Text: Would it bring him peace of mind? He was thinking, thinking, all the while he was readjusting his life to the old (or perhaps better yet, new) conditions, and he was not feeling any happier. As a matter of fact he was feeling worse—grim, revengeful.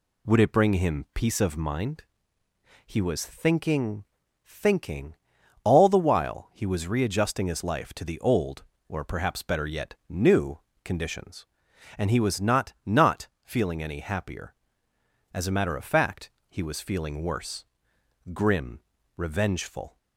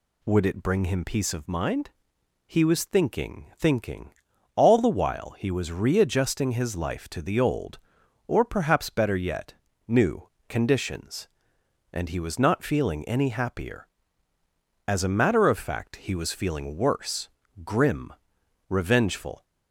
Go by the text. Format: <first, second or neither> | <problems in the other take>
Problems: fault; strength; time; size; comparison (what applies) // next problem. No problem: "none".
second | says "not" twice; at 12.8 s // pauses between "fact" and "he"; slight; at 16.3 s; 0.16 s long